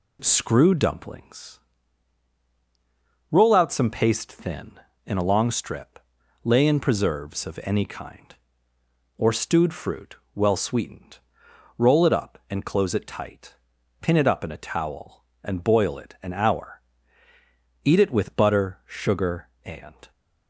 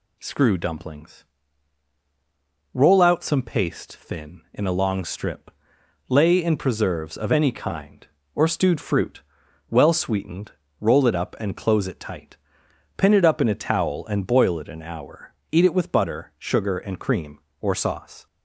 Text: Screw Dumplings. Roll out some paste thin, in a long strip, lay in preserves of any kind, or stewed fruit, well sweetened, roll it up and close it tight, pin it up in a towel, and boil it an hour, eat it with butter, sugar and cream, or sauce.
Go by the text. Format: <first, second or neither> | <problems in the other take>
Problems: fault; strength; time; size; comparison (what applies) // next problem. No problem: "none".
second | stops before "cream or sauce"; at 20.1 s